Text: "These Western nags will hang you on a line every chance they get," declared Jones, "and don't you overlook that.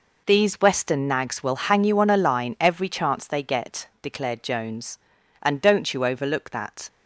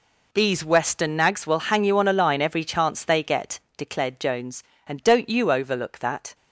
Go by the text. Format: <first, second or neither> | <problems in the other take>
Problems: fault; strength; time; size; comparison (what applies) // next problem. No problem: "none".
neither | none